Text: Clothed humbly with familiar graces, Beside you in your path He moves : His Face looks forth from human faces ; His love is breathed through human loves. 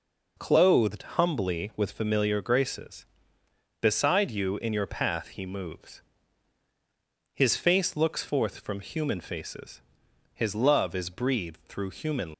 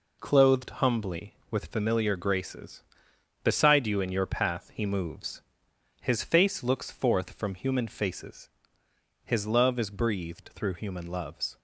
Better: second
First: stops before "loves"; at 12.3 s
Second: none

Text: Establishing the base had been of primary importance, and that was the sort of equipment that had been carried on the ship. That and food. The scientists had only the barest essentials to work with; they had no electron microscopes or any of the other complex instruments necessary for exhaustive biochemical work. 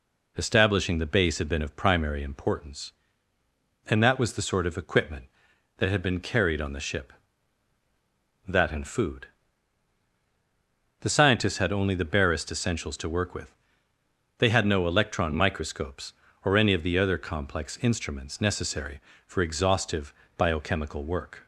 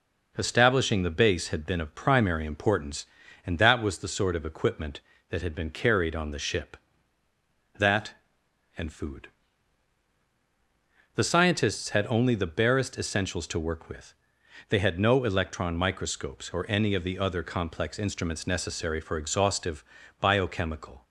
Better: first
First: pauses between "exhaustive" and "biochemical"; slight; at 20.1 s; 0.24 s long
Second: pauses between "exhaustive" and "biochemical"; slight; at 19.8 s; 0.34 s long // stops before "work"; at 21.0 s

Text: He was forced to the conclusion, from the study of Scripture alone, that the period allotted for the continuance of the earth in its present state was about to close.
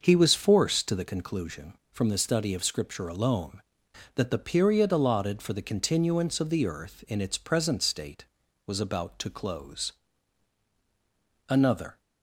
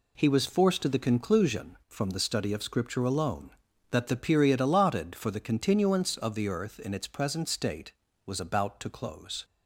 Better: second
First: starts louder than the rest; until 1.0 s; 6.5 dB // goes on to say "Another"; from 11.5 s on; 0.50 s long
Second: none

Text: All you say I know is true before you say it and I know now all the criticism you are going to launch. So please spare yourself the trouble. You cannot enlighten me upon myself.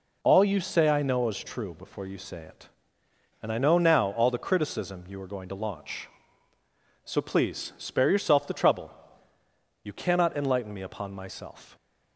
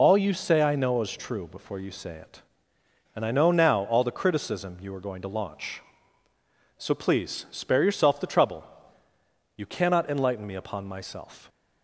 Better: first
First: none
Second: loses the start of "All"; at 0.0 s; 35 ms

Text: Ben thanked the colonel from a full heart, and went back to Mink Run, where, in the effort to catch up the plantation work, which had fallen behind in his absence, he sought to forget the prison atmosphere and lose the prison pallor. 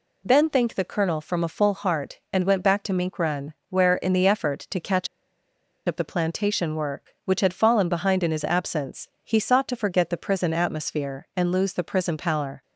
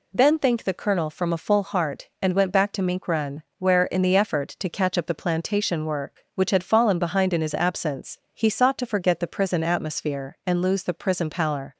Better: second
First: pauses between "catch" and "up"; noticeable; at 5.0 s; 0.80 s long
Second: none

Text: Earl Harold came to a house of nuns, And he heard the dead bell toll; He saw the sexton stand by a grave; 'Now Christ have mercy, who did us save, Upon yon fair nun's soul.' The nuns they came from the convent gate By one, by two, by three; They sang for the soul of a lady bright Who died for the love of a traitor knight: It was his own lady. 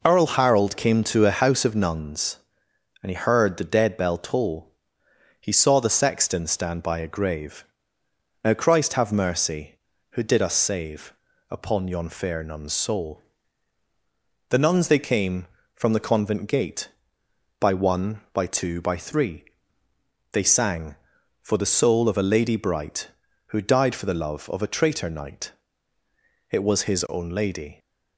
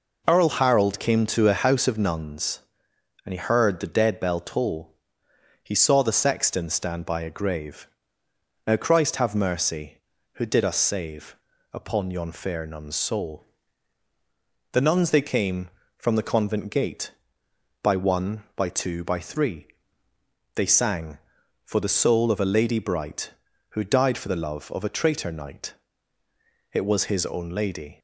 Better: neither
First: none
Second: none

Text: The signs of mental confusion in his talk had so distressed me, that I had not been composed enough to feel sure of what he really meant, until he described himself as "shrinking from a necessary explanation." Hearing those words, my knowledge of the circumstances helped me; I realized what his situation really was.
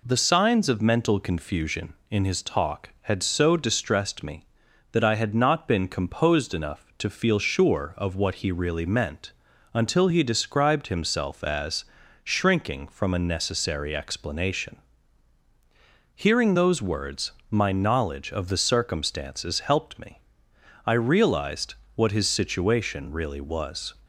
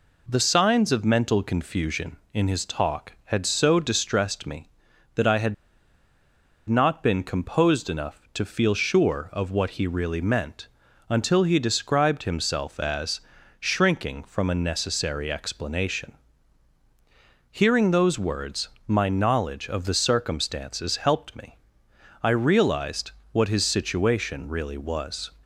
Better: first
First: pauses between "as" and "shrinking"; slight; at 11.8 s; 0.36 s long // pauses between "realized" and "what"; slight; at 21.7 s; 0.20 s long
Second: pauses between "had" and "not"; at 5.5 s; 1.1 s long // pauses between "as" and "shrinking"; slight; at 13.2 s; 0.36 s long // pauses between "realized" and "what"; slight; at 23.1 s; 0.20 s long

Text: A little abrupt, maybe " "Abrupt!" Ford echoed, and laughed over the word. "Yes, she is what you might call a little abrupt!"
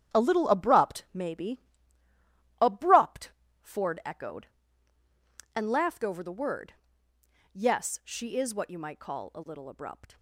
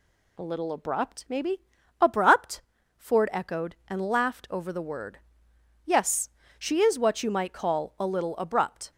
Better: second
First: gets quieter; slight; throughout; 3.5 dB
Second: none

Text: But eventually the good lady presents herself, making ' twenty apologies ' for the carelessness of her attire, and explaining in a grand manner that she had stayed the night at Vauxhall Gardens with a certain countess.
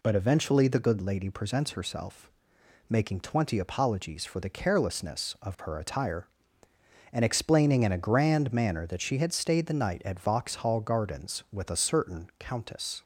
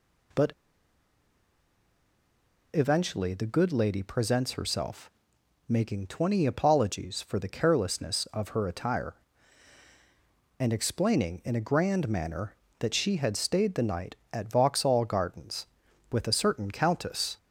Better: first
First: none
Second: pauses between "But" and "eventually"; strong; at 0.5 s; 2.2 s long

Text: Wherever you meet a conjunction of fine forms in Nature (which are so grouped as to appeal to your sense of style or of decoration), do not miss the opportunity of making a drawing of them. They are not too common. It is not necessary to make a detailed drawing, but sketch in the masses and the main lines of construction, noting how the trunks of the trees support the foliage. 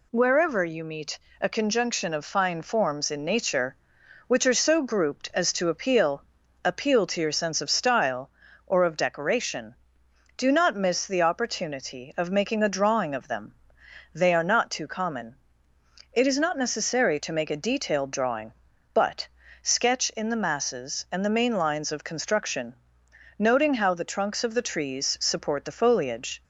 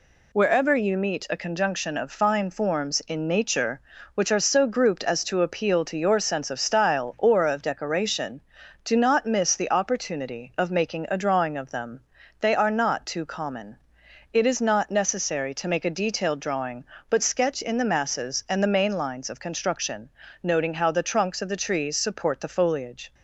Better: second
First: pauses between "meet" and "a"; slight; at 1.1 s; 0.24 s long // says "appeal" twice; at 6.6 s // pauses between "but" and "sketch"; slight; at 19.2 s; 0.36 s long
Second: none

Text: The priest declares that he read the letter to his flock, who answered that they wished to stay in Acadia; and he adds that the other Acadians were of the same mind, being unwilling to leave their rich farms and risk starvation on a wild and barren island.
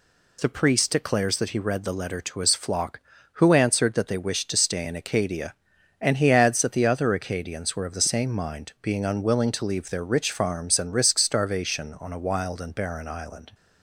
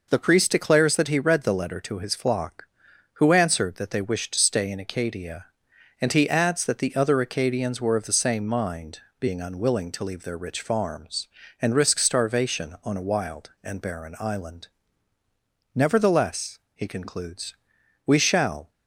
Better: first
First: none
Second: goes on to say "Nevertheless he concludes we shall"; strong; from 15.7 s on; 2.9 s long

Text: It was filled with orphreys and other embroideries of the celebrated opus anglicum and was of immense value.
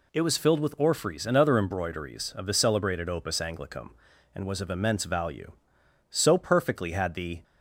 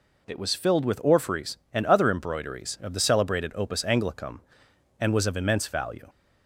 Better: second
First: goes on to say "So perfectly had the"; from 6.0 s on; 1.3 s long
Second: none

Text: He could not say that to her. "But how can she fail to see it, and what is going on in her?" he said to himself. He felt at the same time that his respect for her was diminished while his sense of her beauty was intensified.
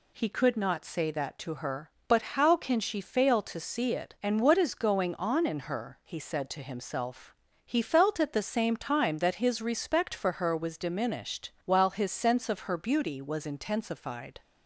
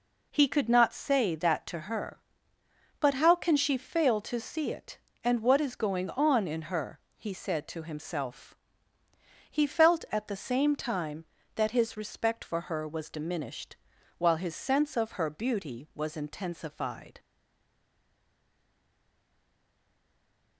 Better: first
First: none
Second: pauses between "diminished" and "while"; at 13.7 s; 0.44 s long // stays silent after the last word; strong; from 17.1 s on; 3.4 s long

